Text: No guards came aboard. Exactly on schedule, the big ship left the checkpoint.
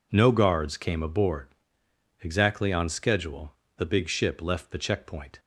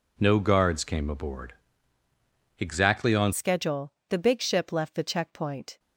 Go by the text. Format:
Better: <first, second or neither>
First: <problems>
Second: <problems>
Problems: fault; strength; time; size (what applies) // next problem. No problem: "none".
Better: first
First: none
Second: changes voice at "schedule"; from 3.3 s on; 2.4 s long